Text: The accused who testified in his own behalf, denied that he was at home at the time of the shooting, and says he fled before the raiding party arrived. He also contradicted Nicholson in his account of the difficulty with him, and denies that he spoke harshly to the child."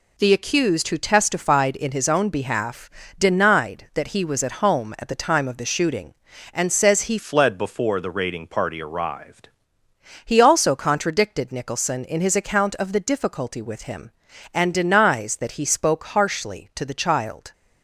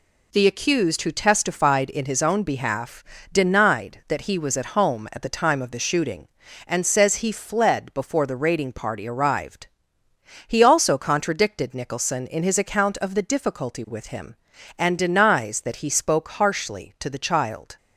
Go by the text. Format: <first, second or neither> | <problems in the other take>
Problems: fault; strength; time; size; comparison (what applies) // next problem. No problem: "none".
second | changes voice from "fled" to "arrived"; from 7.1 to 9.4 s; 2.3 s long